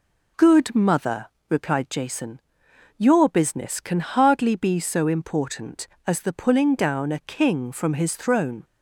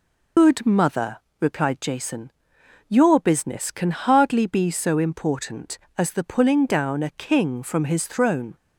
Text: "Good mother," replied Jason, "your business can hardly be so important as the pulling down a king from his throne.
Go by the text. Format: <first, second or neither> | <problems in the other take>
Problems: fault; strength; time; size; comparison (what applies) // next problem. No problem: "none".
first | loses the start of "Good"; at 0.3 s; 100 ms